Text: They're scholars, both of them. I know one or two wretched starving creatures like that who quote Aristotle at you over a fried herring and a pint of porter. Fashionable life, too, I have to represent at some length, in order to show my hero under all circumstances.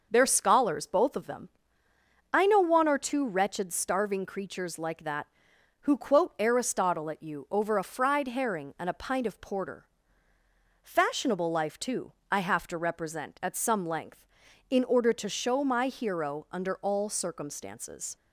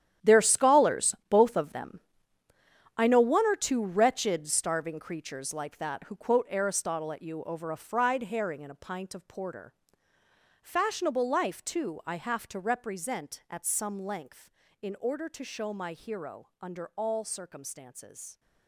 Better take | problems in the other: first | gets quieter; strong; throughout; 13 dB

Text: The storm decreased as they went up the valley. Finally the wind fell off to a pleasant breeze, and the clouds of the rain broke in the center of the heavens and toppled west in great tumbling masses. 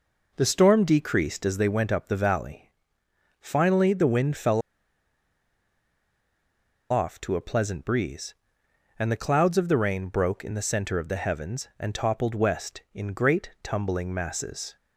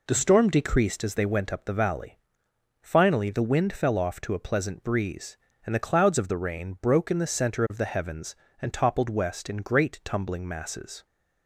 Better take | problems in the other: second | pauses between "fell" and "off"; strong; at 4.6 s; 2.3 s long

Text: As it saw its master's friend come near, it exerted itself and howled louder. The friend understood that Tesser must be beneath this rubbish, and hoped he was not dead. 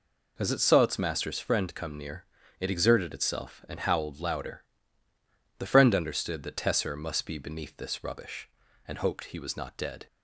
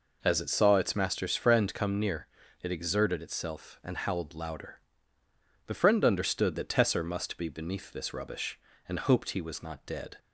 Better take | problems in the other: neither | none

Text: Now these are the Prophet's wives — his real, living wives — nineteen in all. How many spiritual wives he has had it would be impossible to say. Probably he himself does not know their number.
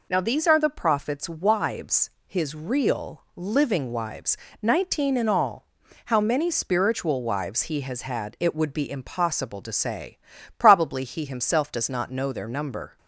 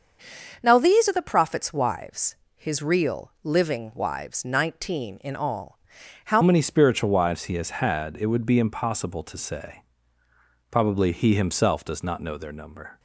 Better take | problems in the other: first | starts louder than the rest; until 1.6 s; 6.5 dB // changes voice at "many"; from 6.4 s on; 6.5 s long

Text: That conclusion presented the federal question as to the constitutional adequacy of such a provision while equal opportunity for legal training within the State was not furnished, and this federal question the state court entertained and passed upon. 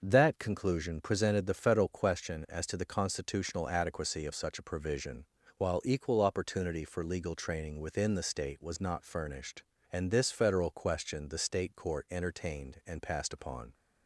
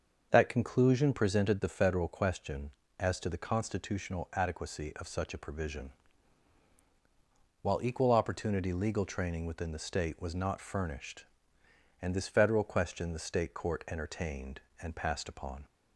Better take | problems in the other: first | starts louder than the rest; until 1.3 s; 6.5 dB; noticeable in the first // pauses between "provision" and "while"; strong; at 5.8 s; 1.7 s long; slight in the first // skips "for"; at 8.7 s

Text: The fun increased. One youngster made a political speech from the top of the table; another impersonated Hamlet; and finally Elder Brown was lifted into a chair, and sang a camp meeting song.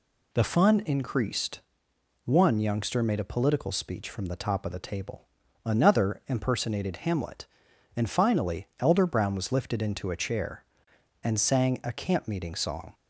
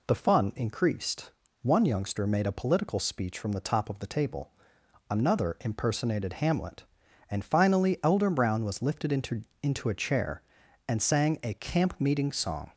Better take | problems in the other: first | says "into" twice; at 9.6 s

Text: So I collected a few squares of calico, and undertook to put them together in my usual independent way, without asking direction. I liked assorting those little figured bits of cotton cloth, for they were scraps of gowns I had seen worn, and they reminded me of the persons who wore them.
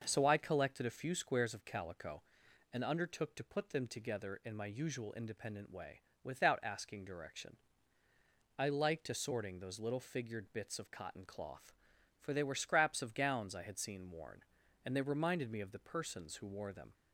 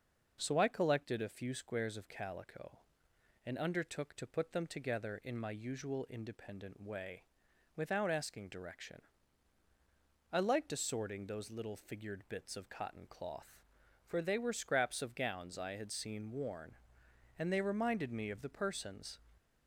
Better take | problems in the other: first | stops before "who wore them"; at 19.3 s

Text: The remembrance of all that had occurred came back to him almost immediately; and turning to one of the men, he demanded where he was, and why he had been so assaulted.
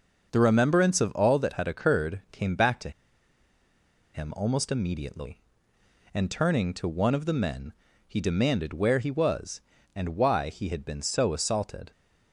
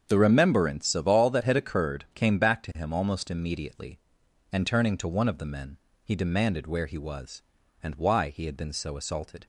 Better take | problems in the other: second | starts louder than the rest; noticeable; until 1.3 s; 6 dB; strong in the second // pauses between "to" and "him"; at 2.8 s; 1.2 s long

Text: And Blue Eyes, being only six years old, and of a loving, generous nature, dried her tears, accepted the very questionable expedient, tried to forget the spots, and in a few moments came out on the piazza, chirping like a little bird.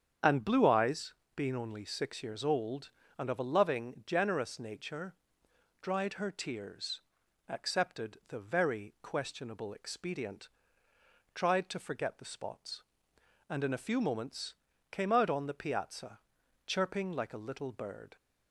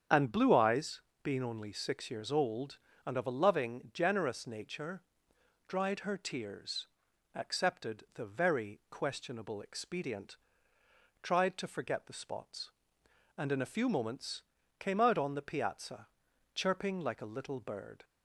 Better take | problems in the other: neither | starts louder than the rest; strong; the same in both // pauses between "moments" and "came"; the same in both

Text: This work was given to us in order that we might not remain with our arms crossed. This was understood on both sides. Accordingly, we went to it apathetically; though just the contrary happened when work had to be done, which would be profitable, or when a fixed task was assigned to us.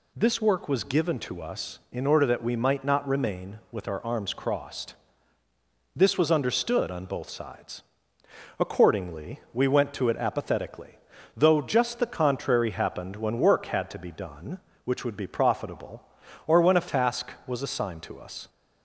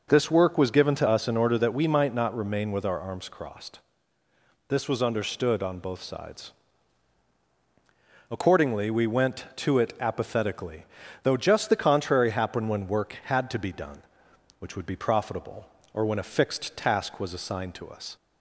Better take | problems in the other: second | skips "fixed"; at 16.8 s

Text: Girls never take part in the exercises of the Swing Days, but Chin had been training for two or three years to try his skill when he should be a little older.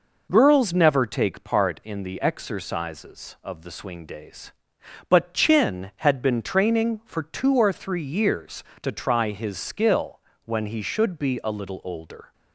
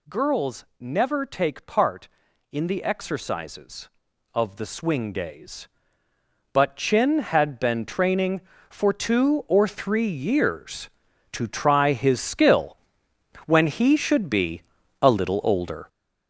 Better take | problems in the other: first | gets louder; strong; throughout; 8 dB // pauses between "skill" and "when"; noticeable; at 12.7 s; 0.70 s long; slight in the first // pauses between "be" and "a"; at 14.6 s; 0.40 s long

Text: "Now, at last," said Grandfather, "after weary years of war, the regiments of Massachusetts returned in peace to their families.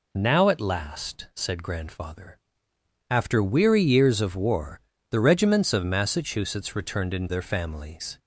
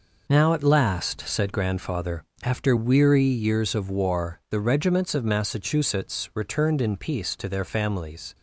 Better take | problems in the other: second | skips "peace to"; at 7.2 s

